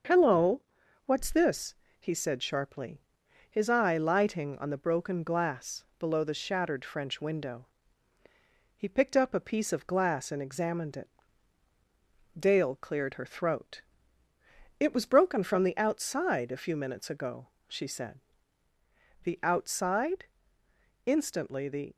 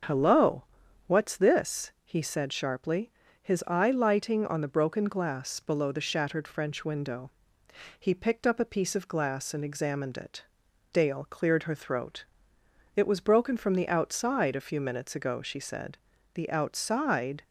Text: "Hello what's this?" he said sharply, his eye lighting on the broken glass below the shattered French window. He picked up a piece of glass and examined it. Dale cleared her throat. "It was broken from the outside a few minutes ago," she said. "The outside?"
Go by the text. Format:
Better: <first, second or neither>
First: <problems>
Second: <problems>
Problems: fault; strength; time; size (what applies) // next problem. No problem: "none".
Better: second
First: starts louder than the rest; until 1.5 s; 6.5 dB // pauses between "Hello" and "what's"; at 0.6 s; 0.44 s long // pauses between "glass" and "below"; slight; at 5.8 s; 0.16 s long // goes on to say "Instantly the"; noticeable; from 21.0 s on; 0.88 s long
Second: starts louder than the rest; strong; until 1.5 s; 7 dB // pauses between "Hello" and "what's"; at 0.6 s; 0.44 s long